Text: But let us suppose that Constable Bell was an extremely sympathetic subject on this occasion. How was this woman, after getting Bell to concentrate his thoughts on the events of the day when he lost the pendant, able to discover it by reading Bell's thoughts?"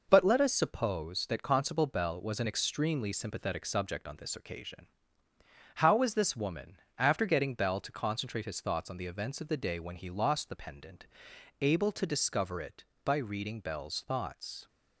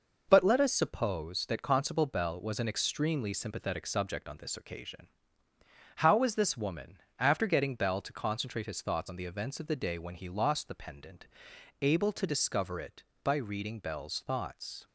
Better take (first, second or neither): neither